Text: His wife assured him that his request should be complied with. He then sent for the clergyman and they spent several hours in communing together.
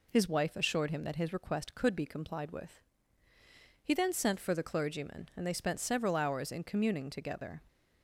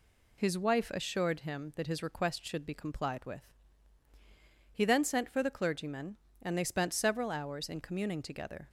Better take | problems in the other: second | says "could" for "should"; at 1.7 s

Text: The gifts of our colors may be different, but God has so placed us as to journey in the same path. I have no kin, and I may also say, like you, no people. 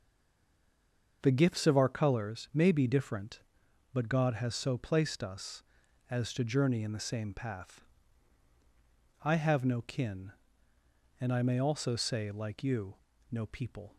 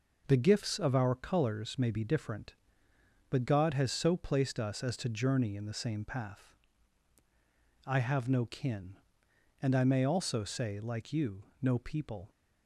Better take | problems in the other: second | stays silent before the first word; noticeable; until 1.2 s; 1.2 s long // starts louder than the rest; until 2.2 s; 6.5 dB

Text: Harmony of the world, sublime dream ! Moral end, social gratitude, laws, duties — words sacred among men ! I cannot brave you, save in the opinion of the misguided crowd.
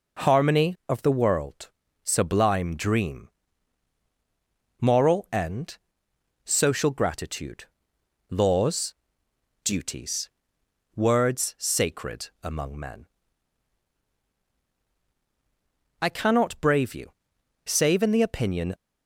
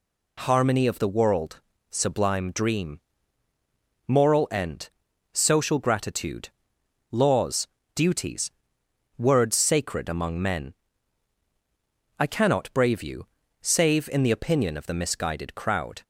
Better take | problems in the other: second | stops before "of the misguided crowd"; at 18.7 s

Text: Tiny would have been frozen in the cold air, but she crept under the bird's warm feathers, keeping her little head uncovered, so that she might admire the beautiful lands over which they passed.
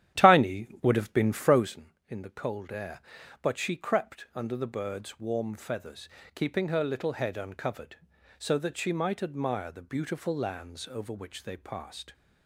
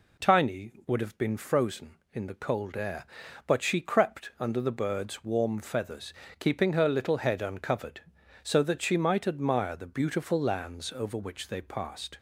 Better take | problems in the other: second | starts louder than the rest; strong; until 1.8 s; 11.5 dB

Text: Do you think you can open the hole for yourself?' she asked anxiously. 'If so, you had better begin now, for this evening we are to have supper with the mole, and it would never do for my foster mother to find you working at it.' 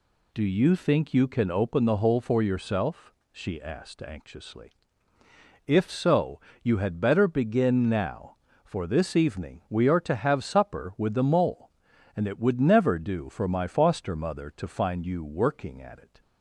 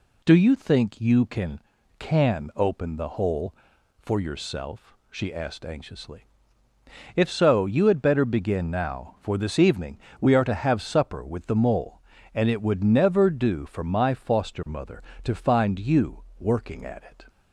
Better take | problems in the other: first | says "can" twice; at 1.9 s // pauses between "evening" and "we"; slight; at 9.9 s; 0.22 s long // pauses between "you" and "working"; slight; at 16.2 s; 0.16 s long

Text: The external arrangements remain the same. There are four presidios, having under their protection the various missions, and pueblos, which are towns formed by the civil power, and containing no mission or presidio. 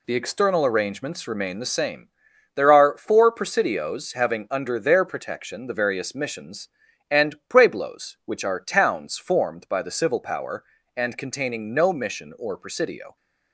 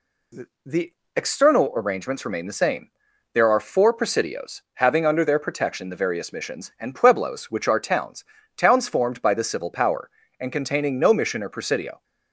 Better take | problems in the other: first | pauses between "The" and "external"; slight; at 0.9 s; 0.22 s long // says "towns" twice; at 8.5 s

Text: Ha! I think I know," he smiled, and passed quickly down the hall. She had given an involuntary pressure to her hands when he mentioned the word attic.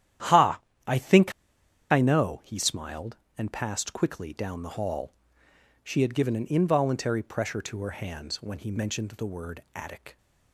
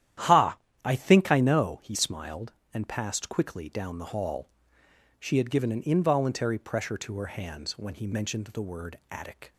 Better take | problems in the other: second | starts louder than the rest; strong; until 2.0 s; 11 dB; strong in the second // pauses between "think" and "I"; noticeable; at 1.3 s; 0.58 s long

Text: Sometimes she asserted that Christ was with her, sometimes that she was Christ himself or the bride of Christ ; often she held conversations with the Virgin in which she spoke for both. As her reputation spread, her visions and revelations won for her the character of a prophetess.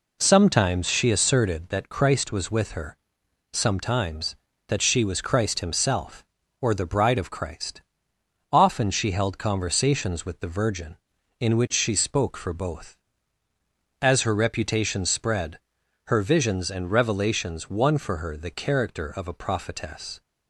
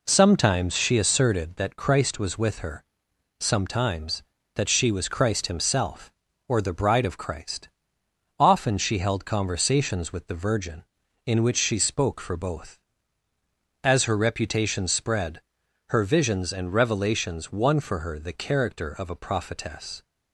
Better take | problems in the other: neither | none

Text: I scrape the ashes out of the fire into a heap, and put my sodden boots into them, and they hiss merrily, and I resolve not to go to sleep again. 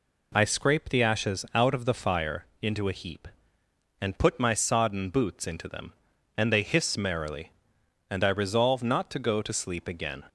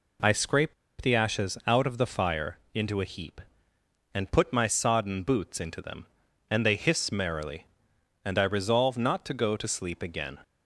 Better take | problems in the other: first | pauses between "scrape" and "the"; slight; at 0.7 s; 0.27 s long

